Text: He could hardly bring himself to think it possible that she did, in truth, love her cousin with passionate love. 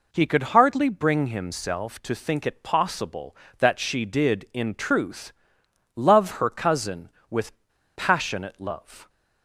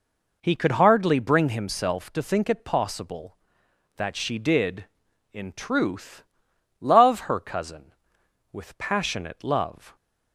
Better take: second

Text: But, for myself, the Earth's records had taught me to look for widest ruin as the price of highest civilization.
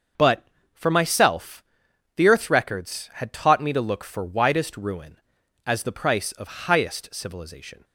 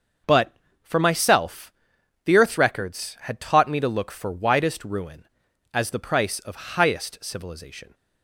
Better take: neither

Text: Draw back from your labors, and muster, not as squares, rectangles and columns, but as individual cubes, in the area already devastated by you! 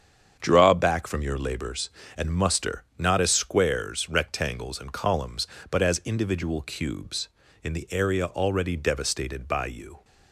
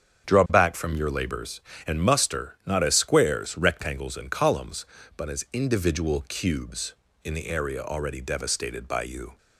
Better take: neither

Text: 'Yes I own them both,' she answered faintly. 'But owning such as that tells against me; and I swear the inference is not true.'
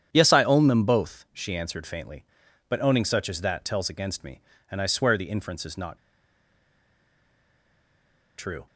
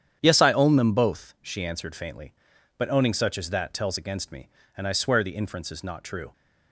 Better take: second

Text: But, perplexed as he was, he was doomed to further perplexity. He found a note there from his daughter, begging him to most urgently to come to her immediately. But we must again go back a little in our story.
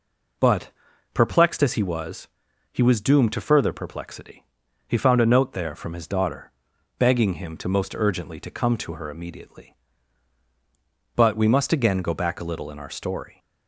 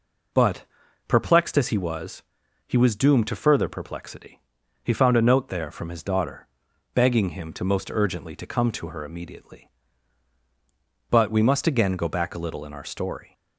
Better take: neither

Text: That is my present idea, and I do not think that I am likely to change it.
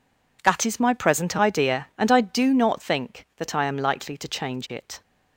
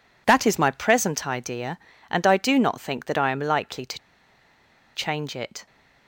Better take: first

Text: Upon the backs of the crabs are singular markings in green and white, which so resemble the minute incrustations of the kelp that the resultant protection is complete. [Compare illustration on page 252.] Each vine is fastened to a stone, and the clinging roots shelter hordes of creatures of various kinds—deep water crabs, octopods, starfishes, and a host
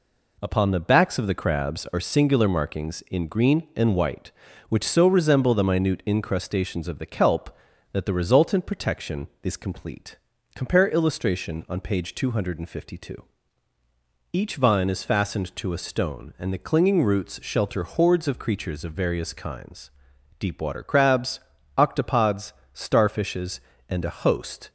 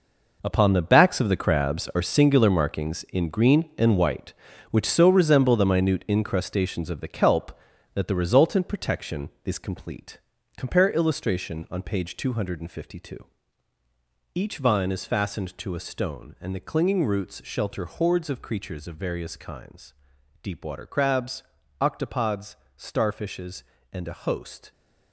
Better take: first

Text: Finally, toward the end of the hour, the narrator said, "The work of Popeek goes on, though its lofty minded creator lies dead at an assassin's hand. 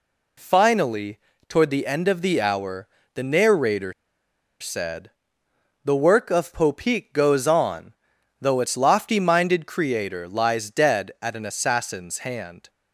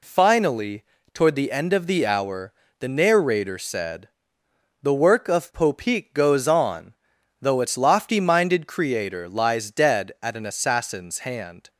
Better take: second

